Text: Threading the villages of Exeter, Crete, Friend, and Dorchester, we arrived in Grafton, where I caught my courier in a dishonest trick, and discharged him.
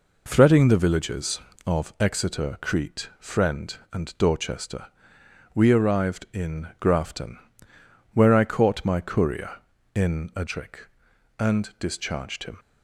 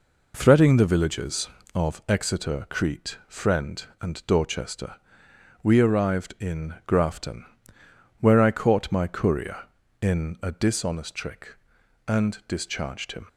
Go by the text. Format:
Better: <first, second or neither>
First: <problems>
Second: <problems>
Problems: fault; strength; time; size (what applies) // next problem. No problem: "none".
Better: second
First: skips "dishonest"; at 10.4 s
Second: none